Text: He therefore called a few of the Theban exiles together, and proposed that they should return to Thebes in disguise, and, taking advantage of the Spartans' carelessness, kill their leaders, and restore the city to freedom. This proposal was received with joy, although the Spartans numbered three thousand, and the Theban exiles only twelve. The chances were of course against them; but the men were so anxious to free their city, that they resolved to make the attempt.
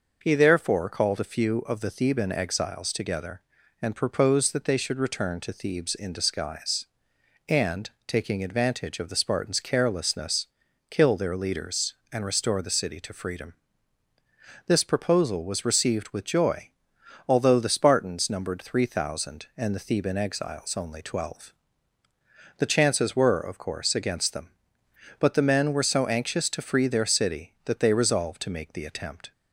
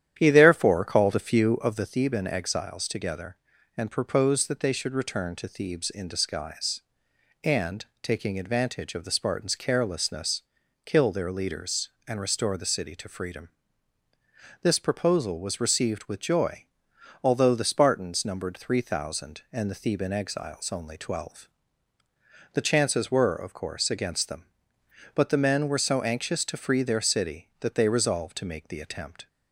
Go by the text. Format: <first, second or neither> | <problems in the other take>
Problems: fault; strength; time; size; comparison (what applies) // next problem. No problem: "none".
first | starts louder than the rest; strong; until 1.9 s; 10.5 dB